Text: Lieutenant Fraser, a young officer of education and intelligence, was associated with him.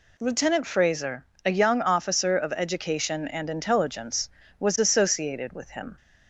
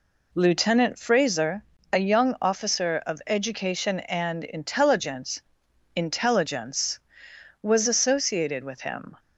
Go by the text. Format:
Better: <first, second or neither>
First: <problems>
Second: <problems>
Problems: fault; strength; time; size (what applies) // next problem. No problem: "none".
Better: first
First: none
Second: says "intelligence" twice; at 5.9 s